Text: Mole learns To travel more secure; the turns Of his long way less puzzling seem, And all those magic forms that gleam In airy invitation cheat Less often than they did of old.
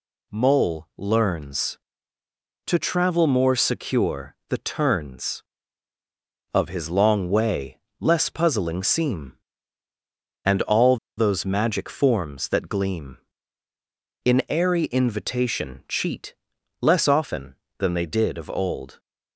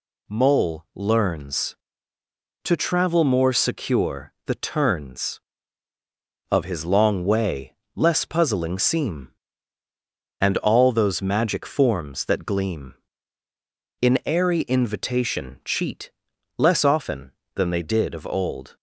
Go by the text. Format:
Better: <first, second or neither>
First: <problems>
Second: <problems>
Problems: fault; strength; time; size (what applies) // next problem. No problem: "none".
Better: second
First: pauses between "way" and "less"; slight; at 7.7 s; 0.22 s long // pauses between "all" and "those"; slight; at 10.9 s; 0.21 s long // pauses between "cheat" and "Less"; at 16.3 s; 0.44 s long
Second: pauses between "way" and "less"; slight; at 7.7 s; 0.22 s long // pauses between "cheat" and "Less"; at 16.1 s; 0.44 s long